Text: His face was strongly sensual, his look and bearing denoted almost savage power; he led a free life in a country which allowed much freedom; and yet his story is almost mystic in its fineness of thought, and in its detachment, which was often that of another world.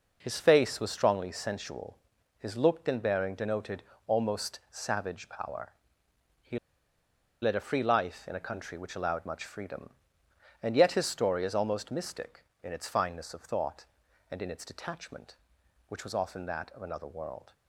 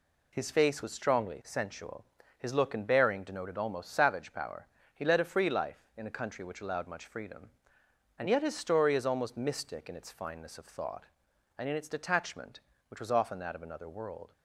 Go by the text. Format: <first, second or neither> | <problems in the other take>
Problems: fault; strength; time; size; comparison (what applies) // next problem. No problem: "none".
second | pauses between "denoted" and "almost"; slight; at 3.8 s; 0.24 s long // pauses between "he" and "led"; noticeable; at 6.5 s; 0.84 s long